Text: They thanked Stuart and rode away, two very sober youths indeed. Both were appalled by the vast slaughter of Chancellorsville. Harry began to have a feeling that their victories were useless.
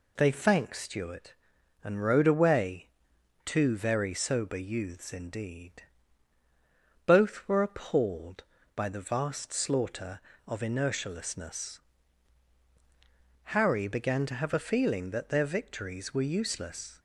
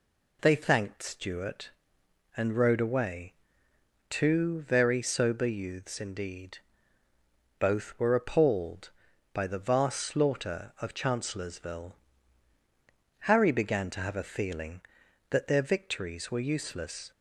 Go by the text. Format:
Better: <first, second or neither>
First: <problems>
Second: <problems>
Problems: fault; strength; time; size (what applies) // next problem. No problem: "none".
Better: second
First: says "Inertialessness" for "Chancellorsville"; at 10.6 s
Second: none